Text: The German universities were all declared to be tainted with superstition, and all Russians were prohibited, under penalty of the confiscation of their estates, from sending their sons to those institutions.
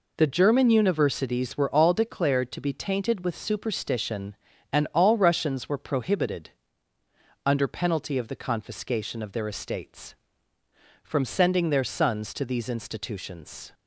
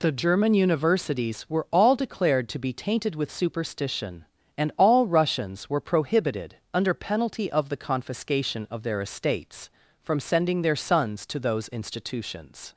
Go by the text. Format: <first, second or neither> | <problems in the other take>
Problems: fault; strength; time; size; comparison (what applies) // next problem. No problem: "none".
second | says "these" for "those"; at 12.4 s